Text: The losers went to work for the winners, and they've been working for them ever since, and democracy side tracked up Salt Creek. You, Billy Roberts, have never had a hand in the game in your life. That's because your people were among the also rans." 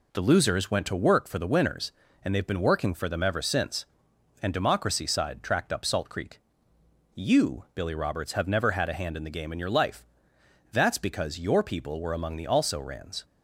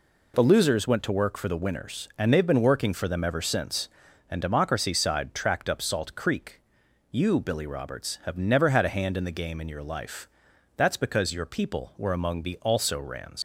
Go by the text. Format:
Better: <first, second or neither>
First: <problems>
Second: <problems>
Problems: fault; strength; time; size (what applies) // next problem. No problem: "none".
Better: first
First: none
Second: leaves "rans" unfinished; at 13.3 s; 105 ms